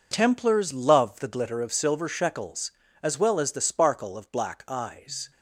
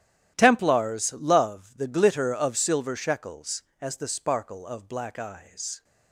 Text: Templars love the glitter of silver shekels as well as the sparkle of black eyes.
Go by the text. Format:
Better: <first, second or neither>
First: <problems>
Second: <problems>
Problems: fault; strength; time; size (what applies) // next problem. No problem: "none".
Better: first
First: none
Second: starts louder than the rest; strong; until 1.3 s; 11.5 dB // skips "as well"; at 3.7 s